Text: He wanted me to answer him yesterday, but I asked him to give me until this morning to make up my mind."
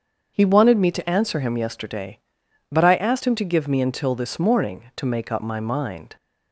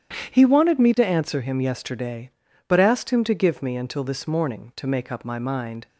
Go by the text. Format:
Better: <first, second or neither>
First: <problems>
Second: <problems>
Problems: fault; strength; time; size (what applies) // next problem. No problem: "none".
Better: first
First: starts louder than the rest; until 1.3 s; 7 dB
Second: starts louder than the rest; strong; until 1.3 s; 9.5 dB // skips "I"; at 2.7 s